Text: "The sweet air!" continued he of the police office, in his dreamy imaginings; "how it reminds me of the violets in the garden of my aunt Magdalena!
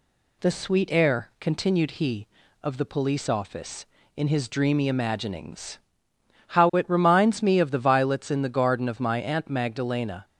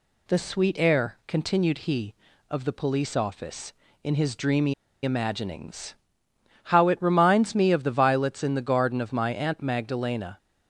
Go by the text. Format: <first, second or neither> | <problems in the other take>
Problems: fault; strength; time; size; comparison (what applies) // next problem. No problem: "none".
first | pauses between "dreamy" and "imaginings"; slight; at 4.7 s; 0.28 s long